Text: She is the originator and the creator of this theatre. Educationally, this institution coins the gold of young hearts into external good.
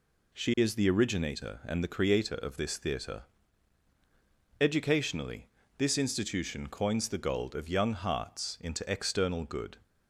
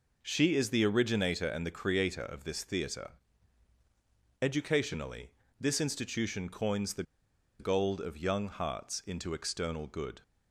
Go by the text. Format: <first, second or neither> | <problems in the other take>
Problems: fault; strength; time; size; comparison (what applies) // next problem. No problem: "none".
first | pauses between "the" and "gold"; noticeable; at 7.0 s; 0.56 s long